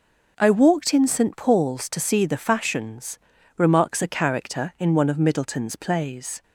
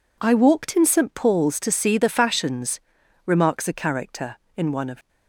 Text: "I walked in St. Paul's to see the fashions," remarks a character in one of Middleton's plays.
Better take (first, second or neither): first